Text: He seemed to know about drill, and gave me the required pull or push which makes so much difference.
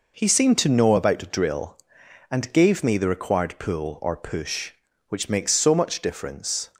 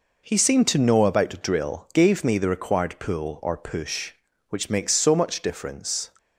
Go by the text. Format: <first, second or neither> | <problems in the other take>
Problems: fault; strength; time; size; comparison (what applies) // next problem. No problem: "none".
first | skips "and"; at 1.9 s